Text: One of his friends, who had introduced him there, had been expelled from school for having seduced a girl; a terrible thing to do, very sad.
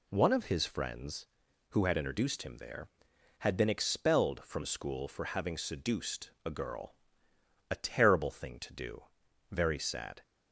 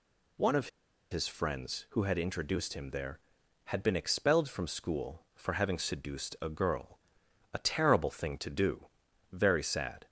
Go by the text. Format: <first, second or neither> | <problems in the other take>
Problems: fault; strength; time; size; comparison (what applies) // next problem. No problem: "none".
first | pauses between "of" and "his"; at 0.6 s; 0.41 s long